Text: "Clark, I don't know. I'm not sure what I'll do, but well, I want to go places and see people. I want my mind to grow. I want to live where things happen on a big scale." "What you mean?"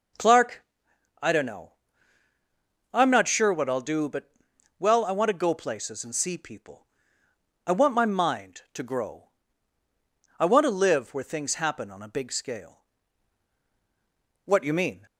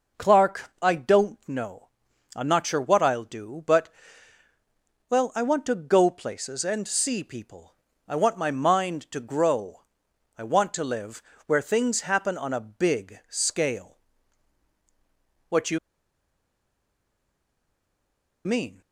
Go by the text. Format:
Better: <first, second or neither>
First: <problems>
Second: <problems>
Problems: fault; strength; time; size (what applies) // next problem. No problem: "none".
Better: first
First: pauses between "but" and "well"; noticeable; at 4.3 s; 0.48 s long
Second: pauses between "but" and "well"; at 3.8 s; 1.2 s long // pauses between "live" and "where"; slight; at 11.2 s; 0.26 s long // pauses between "you" and "mean"; strong; at 15.7 s; 2.6 s long